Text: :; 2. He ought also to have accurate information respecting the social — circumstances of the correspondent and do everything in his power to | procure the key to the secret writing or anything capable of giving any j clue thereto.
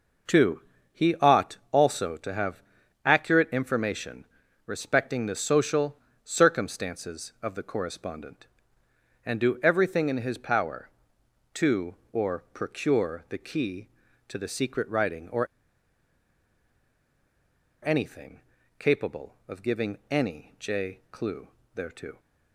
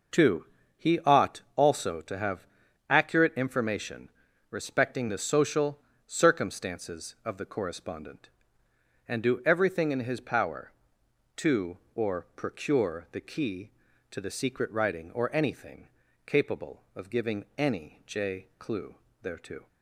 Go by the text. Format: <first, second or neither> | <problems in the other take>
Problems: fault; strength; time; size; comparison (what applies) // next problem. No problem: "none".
second | pauses between "have" and "accurate"; at 2.6 s; 0.44 s long; also in the second // pauses between "information" and "respecting"; at 4.2 s; 0.38 s long; also in the second // pauses between "or" and "anything"; strong; at 15.4 s; 2.3 s long // pauses between "anything" and "capable"; slight; at 18.4 s; 0.36 s long; slight in the second // pauses between "clue" and "thereto"; slight; at 21.4 s; 0.26 s long; slight in the second